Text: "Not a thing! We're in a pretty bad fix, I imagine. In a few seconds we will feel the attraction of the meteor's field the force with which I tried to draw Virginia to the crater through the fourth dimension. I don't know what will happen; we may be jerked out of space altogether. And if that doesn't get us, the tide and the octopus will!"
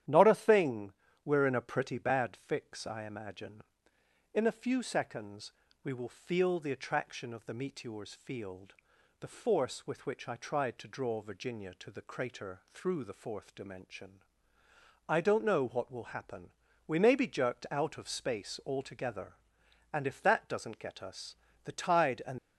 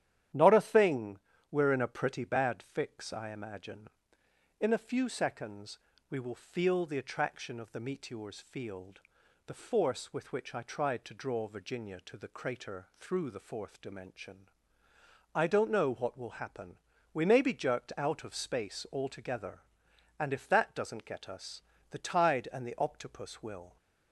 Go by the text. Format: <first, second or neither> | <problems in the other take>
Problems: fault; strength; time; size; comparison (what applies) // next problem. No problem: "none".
second | starts louder than the rest; strong; until 1.4 s; 11 dB; strong in the second // pauses between "seconds" and "we"; slight; at 5.5 s; 0.30 s long; slight in the second // pauses between "field" and "the"; noticeable; at 8.7 s; 0.46 s long; noticeable in the second // stops before "the octopus will"; at 22.3 s